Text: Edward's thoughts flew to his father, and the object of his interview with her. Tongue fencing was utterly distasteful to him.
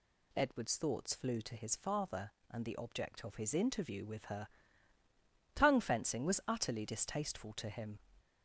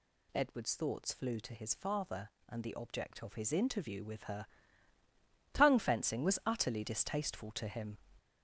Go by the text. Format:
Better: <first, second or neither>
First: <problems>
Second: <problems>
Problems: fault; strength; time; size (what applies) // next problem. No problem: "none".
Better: first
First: none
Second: gets louder; throughout; 6.5 dB